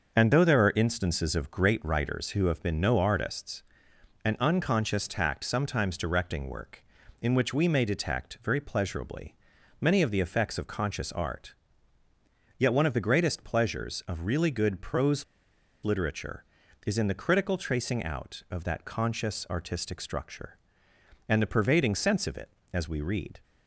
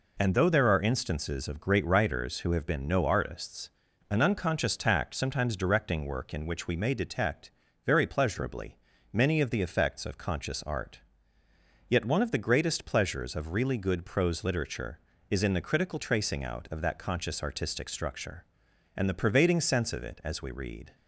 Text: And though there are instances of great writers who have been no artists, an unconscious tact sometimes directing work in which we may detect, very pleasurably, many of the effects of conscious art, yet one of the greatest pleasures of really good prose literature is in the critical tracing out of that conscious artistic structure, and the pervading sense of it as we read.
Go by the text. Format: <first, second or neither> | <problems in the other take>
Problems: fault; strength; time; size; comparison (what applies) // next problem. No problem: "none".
second | starts louder than the rest; until 1.2 s; 6.5 dB // pauses between "prose" and "literature"; noticeable; at 15.2 s; 0.60 s long